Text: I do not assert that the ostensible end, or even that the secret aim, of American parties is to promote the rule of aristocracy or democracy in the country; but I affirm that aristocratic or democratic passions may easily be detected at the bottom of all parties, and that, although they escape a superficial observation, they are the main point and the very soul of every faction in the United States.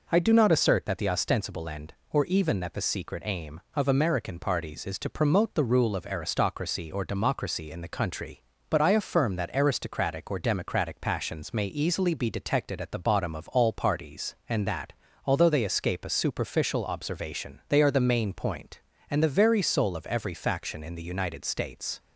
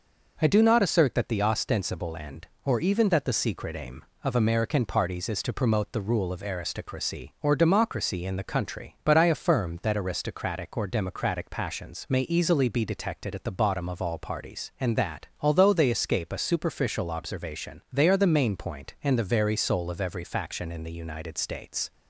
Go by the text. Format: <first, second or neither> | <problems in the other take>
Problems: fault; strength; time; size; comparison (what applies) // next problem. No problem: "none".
neither | none